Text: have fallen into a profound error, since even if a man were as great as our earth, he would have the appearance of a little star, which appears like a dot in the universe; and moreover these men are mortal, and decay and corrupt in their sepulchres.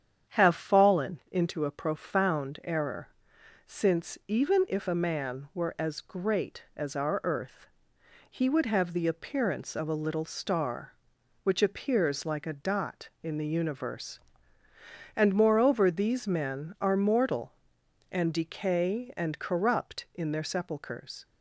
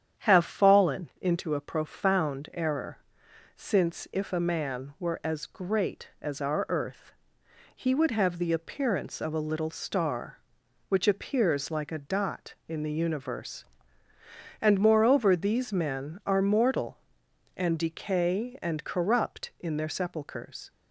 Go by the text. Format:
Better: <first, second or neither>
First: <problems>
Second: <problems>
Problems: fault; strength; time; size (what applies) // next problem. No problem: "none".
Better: first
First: starts louder than the rest; strong; until 1.3 s; 8.5 dB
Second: starts louder than the rest; strong; until 1.2 s; 9 dB // skips "even"; at 4.0 s